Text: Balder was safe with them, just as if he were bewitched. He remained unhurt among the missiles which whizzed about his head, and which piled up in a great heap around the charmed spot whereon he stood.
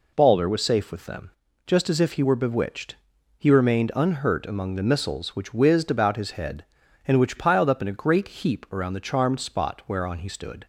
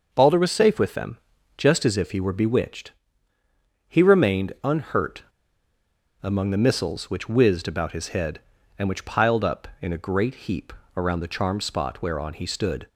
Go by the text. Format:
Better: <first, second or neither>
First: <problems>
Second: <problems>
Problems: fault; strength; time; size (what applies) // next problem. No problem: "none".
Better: first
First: none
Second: pauses between "unhurt" and "among"; at 5.2 s; 0.99 s long // pauses between "heap" and "around"; slight; at 10.7 s; 0.24 s long